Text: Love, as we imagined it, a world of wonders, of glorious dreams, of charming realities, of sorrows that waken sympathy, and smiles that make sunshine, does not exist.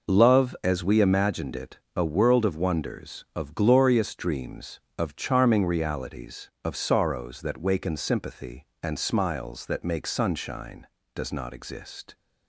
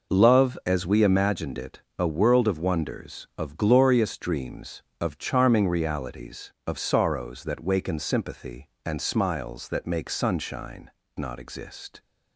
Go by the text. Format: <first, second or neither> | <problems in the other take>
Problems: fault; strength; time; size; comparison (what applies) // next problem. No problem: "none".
first | skips "does"; at 11.0 s